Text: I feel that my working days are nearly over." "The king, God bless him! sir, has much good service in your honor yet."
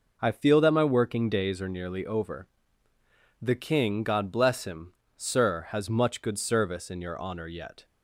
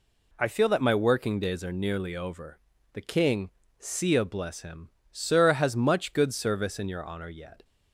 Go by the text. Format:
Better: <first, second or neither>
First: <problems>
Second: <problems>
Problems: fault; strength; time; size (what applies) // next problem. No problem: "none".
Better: first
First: none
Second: says "Sia" for "God"; at 3.7 s